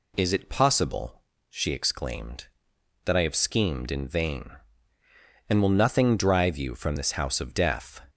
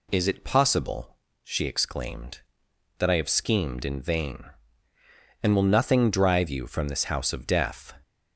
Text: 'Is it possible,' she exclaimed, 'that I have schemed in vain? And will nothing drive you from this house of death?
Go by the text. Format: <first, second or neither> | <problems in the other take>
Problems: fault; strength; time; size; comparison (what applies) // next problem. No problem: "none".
neither | none